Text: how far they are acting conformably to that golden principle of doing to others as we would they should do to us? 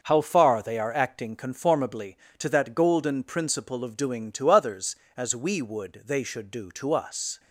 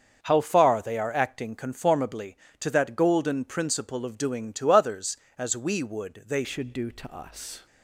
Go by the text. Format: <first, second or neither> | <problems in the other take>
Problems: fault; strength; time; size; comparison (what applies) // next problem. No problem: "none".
first | starts louder than the rest; until 1.2 s; 6.5 dB; noticeable in the first // changes voice at "should"; from 6.4 s on; 1.2 s long